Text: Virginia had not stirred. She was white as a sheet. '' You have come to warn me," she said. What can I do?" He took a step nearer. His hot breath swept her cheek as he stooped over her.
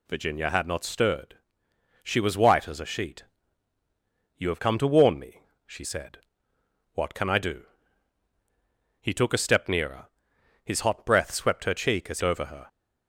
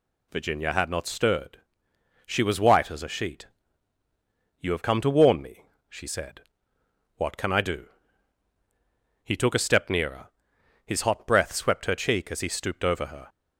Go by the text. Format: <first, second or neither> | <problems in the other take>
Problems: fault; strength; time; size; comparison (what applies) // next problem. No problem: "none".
second | skips "he stooped"; at 12.2 s